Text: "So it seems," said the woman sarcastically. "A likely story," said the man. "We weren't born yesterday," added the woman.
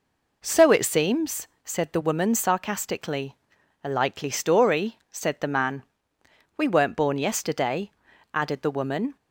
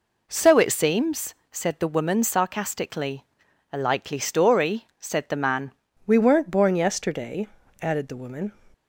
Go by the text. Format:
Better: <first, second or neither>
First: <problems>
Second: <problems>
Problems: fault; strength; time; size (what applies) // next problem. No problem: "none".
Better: first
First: none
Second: changes voice at "We"; from 6.0 s on; 2.5 s long